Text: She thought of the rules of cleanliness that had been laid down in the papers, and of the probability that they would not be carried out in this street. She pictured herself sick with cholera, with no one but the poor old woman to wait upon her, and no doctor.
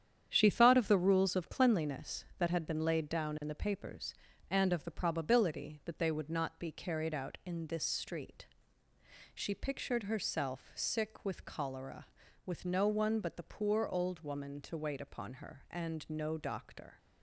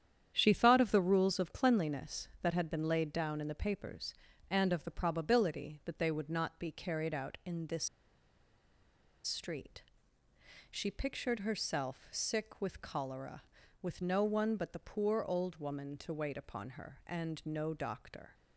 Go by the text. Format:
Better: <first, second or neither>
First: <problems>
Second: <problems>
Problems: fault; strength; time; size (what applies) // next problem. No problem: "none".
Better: first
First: starts louder than the rest; strong; until 1.3 s; 9 dB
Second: starts louder than the rest; strong; until 1.3 s; 9 dB // pauses between "this" and "street"; strong; at 7.8 s; 1.3 s long